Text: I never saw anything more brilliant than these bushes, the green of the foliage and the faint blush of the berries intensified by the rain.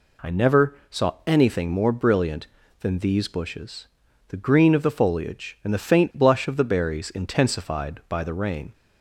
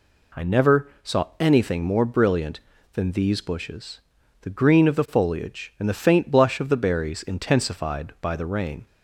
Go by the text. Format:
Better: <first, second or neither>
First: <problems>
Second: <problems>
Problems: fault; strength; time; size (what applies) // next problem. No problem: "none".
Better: neither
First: pauses between "never" and "saw"; slight; at 0.7 s; 0.16 s long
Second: pauses between "never" and "saw"; slight; at 0.8 s; 0.16 s long